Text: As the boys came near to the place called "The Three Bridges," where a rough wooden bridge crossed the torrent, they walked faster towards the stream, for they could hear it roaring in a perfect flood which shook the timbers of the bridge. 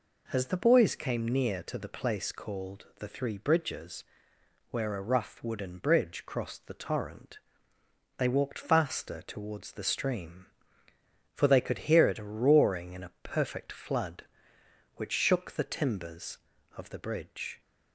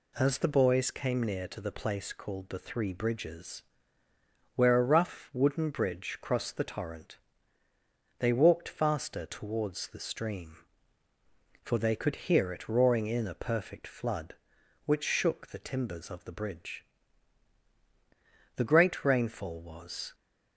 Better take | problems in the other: first | goes on to say "The great rainfall was"; from 18.5 s on; 1.5 s long

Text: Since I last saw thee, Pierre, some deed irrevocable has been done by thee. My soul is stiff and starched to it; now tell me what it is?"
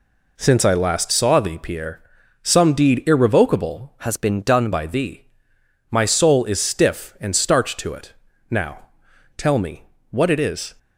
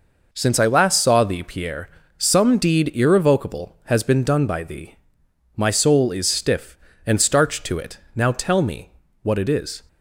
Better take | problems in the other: second | changes voice from "has" to "done"; from 4.0 to 4.7 s; 0.7 s long // pauses between "now" and "tell"; noticeable; at 8.8 s; 0.50 s long // pauses between "me" and "what"; slight; at 9.8 s; 0.26 s long; slight in the second

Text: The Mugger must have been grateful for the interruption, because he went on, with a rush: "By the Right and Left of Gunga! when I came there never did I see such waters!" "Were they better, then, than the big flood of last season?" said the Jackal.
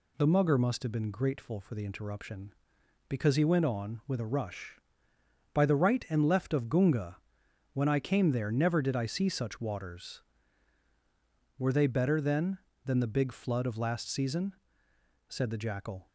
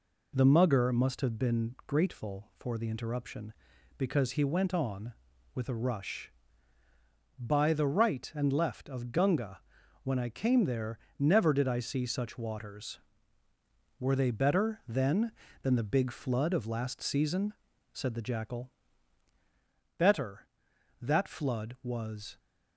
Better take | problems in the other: first | pauses between "there" and "never"; slight; at 10.9 s; 0.22 s long // goes on to say "Better That flood was"; strong; from 19.9 s on; 2.4 s long

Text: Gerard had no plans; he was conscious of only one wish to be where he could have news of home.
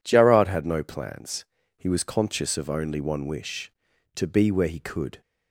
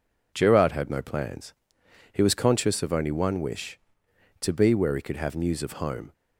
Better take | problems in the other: second | stops before "have news of home"; at 5.2 s

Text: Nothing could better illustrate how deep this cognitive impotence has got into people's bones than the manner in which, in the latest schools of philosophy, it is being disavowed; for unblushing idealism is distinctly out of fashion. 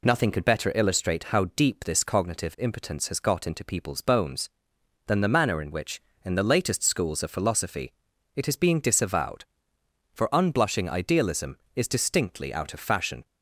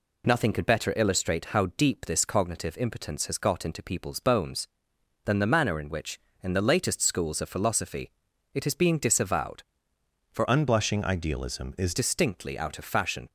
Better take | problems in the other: first | changes voice from "unblushing" to "is"; from 10.4 to 11.9 s; 1.5 s long

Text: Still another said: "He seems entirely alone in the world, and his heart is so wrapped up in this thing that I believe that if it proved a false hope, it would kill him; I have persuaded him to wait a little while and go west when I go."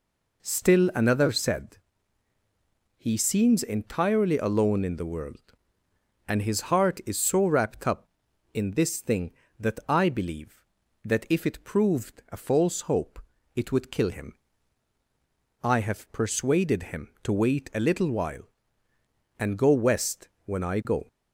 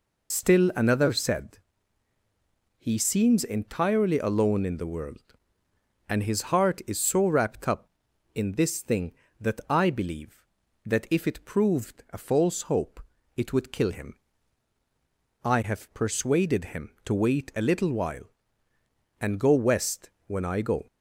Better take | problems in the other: first | loses the start of "Still"; at 0.3 s; 70 ms // pauses between "west" and "when"; slight; at 20.1 s; 0.16 s long; slight in the first

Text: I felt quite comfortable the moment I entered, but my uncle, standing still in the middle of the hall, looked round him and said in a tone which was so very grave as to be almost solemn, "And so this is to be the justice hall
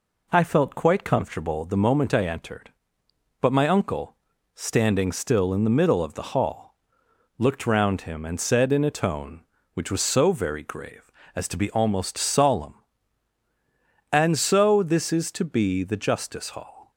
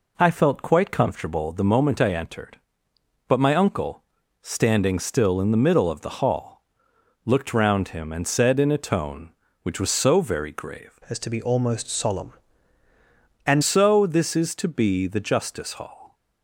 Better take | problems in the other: first | changes voice from "as" to "And"; from 11.0 to 13.6 s; 2.6 s long

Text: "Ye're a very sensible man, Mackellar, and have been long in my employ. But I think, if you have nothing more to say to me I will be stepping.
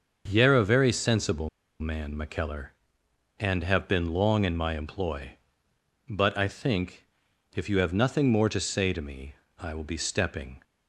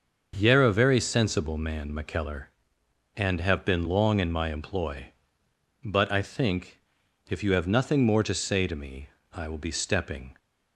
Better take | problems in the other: second | starts louder than the rest; until 1.2 s; 6.5 dB; also in the second // pauses between "sensible" and "man"; slight; at 1.4 s; 0.31 s long // pauses between "me" and "I"; slight; at 9.3 s; 0.24 s long; slight in the second

